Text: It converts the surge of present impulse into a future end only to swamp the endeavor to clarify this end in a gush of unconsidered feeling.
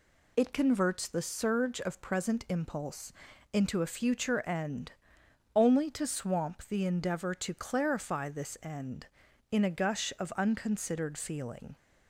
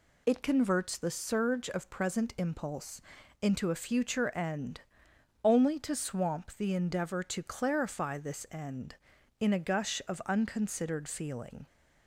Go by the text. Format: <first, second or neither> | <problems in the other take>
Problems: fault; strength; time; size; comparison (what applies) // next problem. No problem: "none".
neither | pauses between "impulse" and "into"; the same in both // pauses between "end" and "only"; noticeable; the same in both